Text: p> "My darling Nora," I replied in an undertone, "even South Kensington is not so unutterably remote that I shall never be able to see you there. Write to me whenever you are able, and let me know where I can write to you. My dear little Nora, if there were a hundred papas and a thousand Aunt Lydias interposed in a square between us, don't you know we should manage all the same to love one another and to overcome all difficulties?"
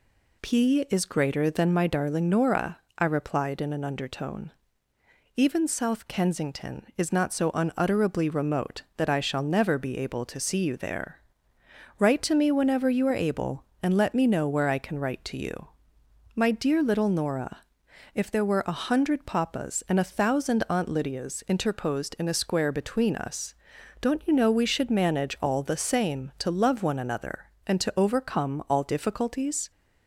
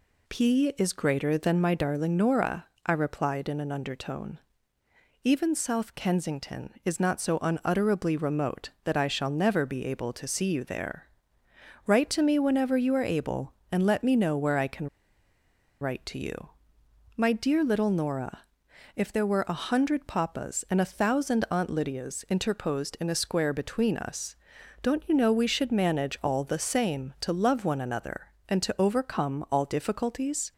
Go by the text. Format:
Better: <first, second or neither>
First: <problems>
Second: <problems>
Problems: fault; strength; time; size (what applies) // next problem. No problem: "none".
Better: first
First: none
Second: pauses between "can" and "write"; noticeable; at 14.8 s; 0.93 s long